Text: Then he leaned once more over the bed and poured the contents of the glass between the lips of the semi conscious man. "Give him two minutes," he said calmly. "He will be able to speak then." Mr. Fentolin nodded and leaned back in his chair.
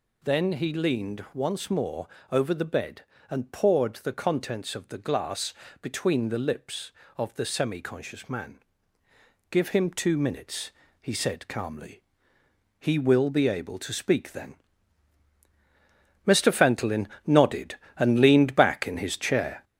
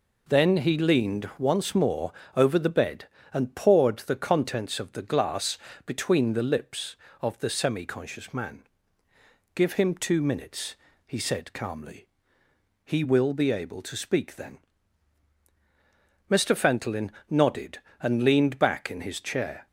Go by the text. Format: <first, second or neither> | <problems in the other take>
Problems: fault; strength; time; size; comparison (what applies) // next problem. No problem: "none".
second | gets louder; noticeable; throughout; 4.5 dB // pauses between "more" and "over"; slight; at 2.0 s; 0.22 s long; slight in the second // pauses between "glass" and "between"; slight; at 5.5 s; 0.28 s long; slight in the second // pauses between "Fentolin" and "nodded"; slight; at 17.0 s; 0.18 s long; slight in the second